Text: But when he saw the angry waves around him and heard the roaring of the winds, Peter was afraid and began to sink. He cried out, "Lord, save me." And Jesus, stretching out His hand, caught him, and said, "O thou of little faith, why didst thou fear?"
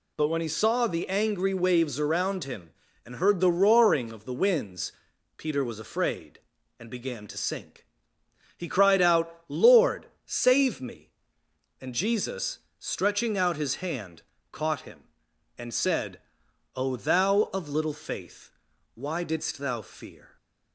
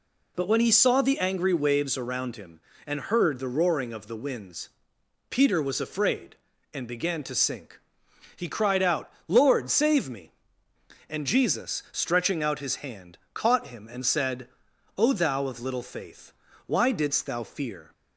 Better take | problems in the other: neither | none

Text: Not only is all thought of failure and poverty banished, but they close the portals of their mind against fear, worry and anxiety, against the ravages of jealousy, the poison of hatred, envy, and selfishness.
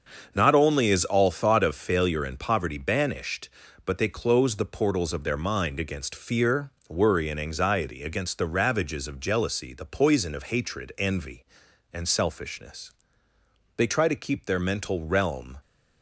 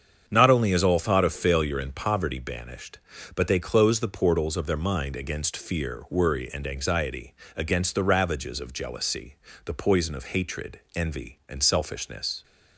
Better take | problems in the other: second | starts louder than the rest; until 1.3 s; 6.5 dB; strong in the second // goes on to say "They try to keep their mental realm"; strong; from 13.7 s on; 1.8 s long

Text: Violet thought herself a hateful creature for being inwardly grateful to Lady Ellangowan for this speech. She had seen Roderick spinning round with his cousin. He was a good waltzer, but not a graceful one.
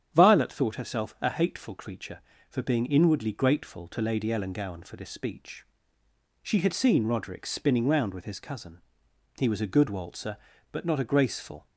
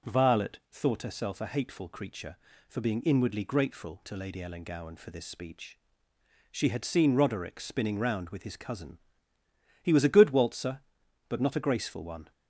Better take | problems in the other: second | starts louder than the rest; strong; until 1.1 s; 9 dB // stops before "one"; at 11.6 s

